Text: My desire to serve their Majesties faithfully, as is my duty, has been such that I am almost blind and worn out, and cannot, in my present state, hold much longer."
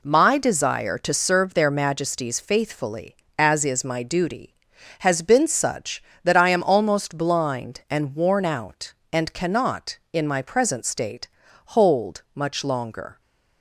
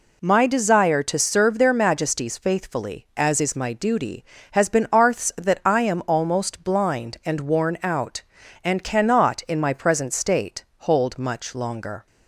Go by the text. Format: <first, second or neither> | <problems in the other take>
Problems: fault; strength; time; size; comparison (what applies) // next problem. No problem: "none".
first | says "arths" for "such"; at 4.9 s